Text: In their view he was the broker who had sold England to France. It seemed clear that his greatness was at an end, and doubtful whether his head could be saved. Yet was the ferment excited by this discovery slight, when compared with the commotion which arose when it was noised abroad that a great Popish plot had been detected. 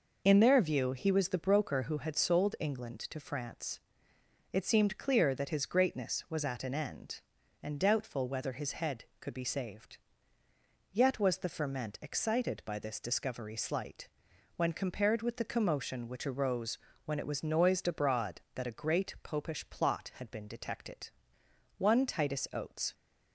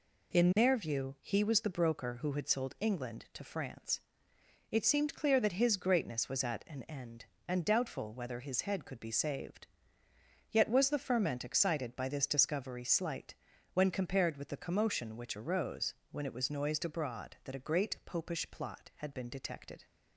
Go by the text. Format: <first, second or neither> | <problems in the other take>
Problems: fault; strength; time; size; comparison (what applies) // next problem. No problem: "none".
second | pauses between "arose" and "when"; slight; at 16.7 s; 0.28 s long; slight in the second // goes on to say "One Titus Oates"; noticeable; from 21.7 s on; 1.1 s long